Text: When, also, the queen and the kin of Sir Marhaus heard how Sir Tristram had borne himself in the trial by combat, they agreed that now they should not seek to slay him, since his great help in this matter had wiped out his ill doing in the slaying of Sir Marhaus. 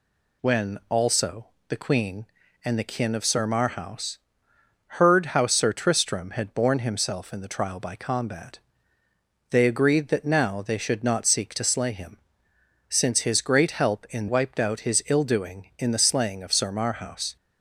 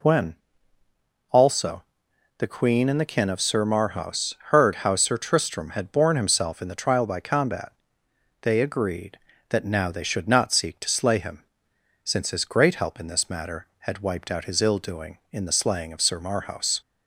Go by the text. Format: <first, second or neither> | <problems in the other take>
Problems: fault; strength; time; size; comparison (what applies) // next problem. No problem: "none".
second | pauses between "Marhaus" and "heard"; noticeable; at 4.1 s; 0.76 s long; slight in the second // skips "this matter had"; at 14.2 s